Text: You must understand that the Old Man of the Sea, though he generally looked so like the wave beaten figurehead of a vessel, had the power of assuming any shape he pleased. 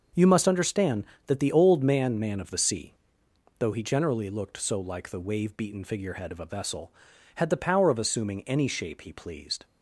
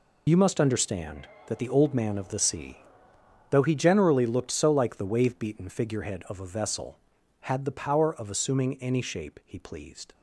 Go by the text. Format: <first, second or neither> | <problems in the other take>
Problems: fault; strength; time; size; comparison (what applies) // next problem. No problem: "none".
second | says "Man" twice; at 2.2 s